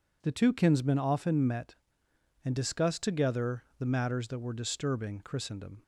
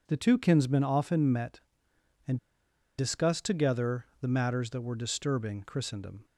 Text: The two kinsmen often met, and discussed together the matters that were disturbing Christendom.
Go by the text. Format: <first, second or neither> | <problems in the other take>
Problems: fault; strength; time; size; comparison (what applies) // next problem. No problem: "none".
first | pauses between "and" and "discussed"; noticeable; at 2.3 s; 0.61 s long // pauses between "together" and "the"; slight; at 4.0 s; 0.16 s long; slight in the first